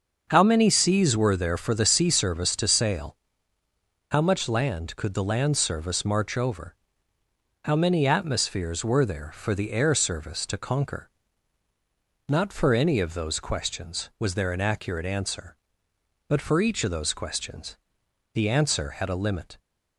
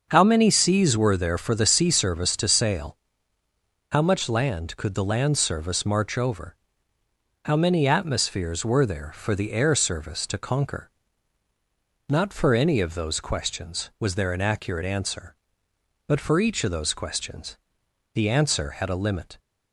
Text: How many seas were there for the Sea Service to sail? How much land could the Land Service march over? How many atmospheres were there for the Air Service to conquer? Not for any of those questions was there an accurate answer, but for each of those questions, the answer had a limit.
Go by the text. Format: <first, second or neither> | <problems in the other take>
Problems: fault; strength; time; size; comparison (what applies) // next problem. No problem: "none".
neither | starts louder than the rest; the same in both